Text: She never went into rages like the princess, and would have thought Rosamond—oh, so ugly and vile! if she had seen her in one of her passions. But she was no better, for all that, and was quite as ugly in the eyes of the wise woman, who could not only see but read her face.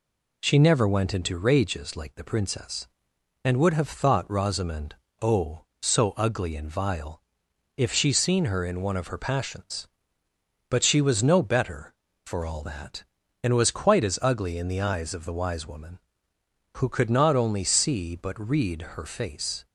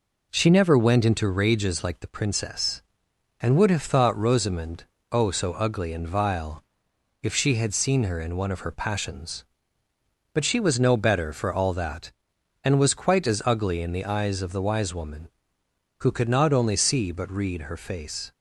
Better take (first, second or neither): second